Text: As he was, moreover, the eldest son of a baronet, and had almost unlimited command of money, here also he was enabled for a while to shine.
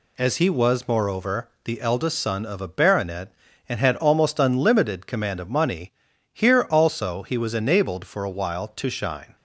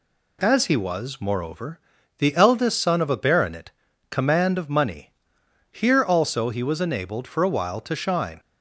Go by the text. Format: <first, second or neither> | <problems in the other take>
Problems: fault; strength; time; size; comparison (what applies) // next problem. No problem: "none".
first | skips "and had almost unlimited"; at 3.9 s